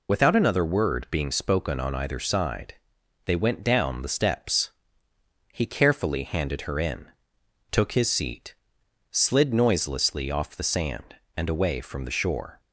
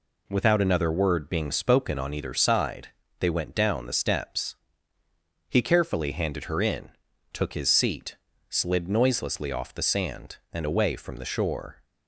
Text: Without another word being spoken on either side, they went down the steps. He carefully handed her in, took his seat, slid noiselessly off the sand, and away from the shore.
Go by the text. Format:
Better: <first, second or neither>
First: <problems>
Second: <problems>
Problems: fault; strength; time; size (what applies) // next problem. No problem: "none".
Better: second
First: loses the start of "Without"; at 0.0 s; 65 ms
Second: none